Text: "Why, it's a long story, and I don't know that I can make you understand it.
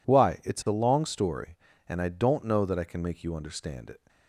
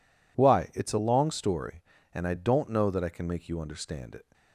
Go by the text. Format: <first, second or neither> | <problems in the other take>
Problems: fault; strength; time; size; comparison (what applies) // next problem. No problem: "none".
neither | none